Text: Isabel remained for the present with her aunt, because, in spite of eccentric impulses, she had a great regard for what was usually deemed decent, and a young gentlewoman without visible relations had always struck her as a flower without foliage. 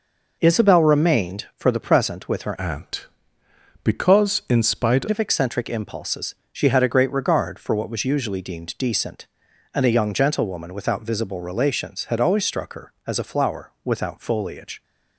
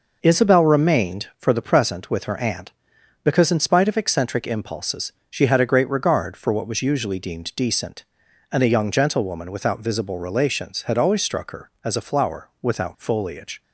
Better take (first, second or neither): second